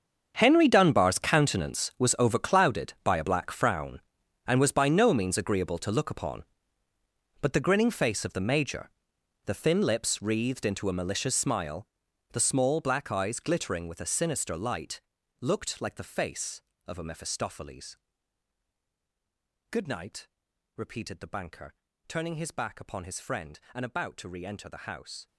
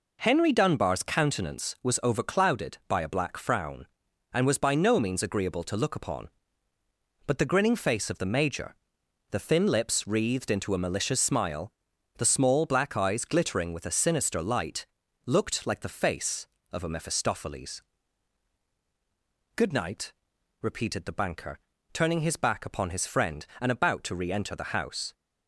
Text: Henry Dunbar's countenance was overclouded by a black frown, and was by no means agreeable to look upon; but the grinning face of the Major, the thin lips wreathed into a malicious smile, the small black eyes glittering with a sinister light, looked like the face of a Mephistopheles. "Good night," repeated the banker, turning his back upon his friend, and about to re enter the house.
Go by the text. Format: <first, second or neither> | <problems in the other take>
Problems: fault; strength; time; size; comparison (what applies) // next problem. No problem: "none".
second | gets quieter; strong; throughout; 17 dB